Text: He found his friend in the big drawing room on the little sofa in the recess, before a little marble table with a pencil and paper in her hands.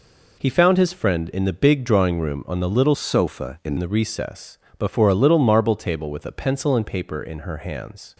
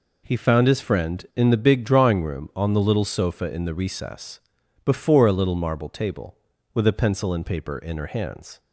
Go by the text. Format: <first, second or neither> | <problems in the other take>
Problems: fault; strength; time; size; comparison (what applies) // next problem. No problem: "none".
second | changes voice from "sofa" to "in"; from 2.9 to 3.7 s; 0.8 s long